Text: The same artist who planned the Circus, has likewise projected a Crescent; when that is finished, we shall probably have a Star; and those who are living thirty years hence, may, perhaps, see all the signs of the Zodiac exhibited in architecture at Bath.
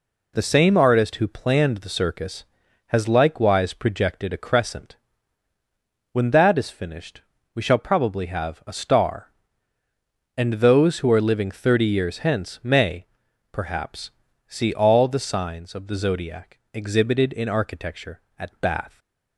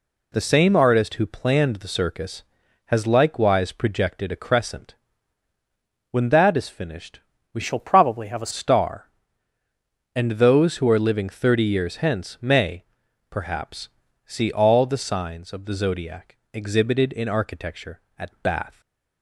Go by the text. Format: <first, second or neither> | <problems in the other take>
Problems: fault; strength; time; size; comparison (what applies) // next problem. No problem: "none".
first | changes voice from "shall" to "a"; from 7.6 to 8.5 s; 0.9 s long // pauses between "Zodiac" and "exhibited"; slight; at 16.3 s; 0.16 s long // stays silent after the last word; slight; from 18.7 s on; 0.5 s long